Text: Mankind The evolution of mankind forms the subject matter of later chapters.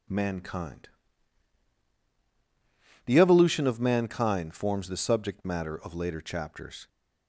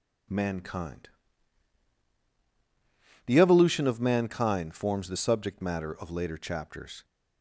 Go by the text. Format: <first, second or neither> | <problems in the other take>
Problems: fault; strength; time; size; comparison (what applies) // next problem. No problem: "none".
neither | pauses between "Mankind" and "The"; strong; the same in both